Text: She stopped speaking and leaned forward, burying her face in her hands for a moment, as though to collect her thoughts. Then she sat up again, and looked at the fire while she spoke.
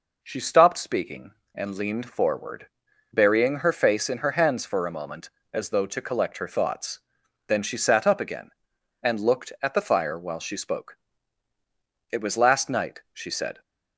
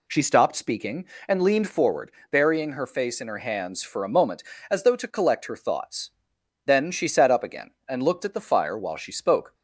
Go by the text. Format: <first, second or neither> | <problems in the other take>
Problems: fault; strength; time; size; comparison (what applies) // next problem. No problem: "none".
second | goes on to say "It was last night she said"; from 12.1 s on; 1.5 s long